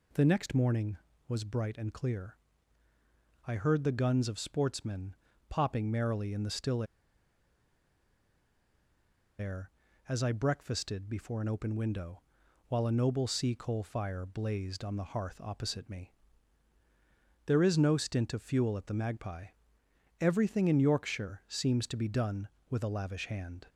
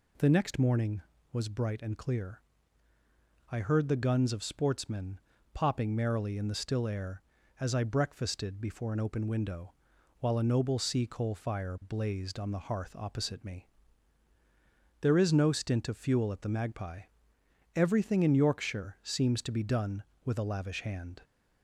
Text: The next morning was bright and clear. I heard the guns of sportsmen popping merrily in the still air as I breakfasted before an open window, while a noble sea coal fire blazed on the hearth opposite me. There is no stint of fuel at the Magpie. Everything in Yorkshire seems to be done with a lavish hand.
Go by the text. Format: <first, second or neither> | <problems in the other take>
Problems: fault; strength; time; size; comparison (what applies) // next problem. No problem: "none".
second | pauses between "sportsmen" and "popping"; slight; at 5.1 s; 0.32 s long; slight in the second // pauses between "still" and "air"; strong; at 6.8 s; 2.5 s long